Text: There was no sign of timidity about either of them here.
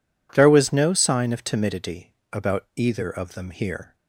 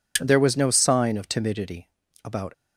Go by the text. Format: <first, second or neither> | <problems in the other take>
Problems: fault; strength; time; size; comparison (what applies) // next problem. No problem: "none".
first | pauses between "timidity" and "about"; slight; at 1.8 s; 0.36 s long; slight in the first // stops before "either of them here"; at 2.5 s